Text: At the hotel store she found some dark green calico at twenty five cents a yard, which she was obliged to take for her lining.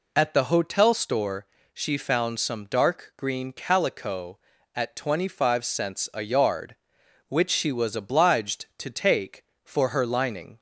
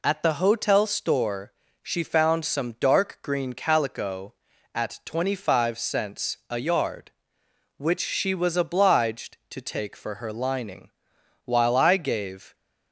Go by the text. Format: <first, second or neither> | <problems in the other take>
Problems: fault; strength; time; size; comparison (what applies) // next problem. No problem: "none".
first | pauses between "store" and "she"; slight; at 1.5 s; 0.30 s long; slight in the first // goes on to say "While I gave"; noticeable; from 11.4 s on; 1.1 s long